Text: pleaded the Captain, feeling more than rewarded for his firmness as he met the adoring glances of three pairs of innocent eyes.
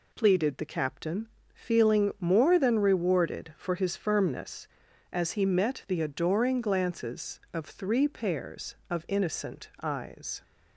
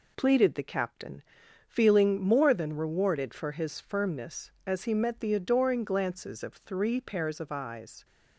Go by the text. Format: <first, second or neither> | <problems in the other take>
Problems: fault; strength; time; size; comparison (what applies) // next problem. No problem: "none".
first | skips "innocent"; at 7.5 s